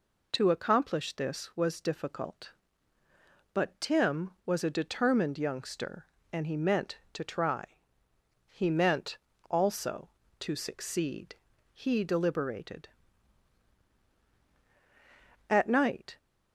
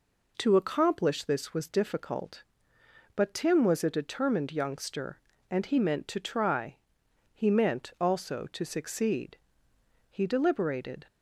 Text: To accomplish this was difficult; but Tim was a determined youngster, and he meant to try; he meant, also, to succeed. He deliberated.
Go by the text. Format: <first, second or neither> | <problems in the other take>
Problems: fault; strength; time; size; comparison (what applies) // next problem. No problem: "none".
second | goes on to say "At night"; noticeable; from 15.4 s on; 0.68 s long